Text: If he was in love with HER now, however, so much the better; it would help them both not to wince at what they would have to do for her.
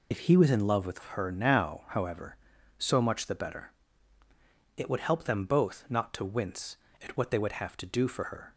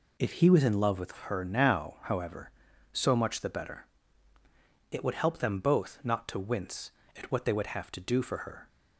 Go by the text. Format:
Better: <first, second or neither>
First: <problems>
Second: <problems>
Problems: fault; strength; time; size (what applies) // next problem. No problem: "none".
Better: second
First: loses the start of "If"; at 0.1 s; 45 ms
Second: none